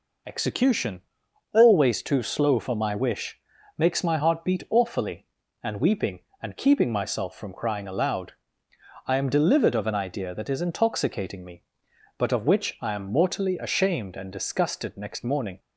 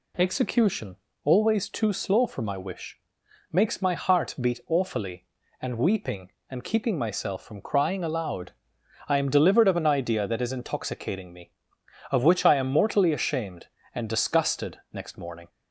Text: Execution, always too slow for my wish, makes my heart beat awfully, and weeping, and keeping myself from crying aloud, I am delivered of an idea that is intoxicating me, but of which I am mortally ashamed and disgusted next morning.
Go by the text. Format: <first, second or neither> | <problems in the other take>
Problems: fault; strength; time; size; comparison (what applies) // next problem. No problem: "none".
first | skips "but"; at 11.8 s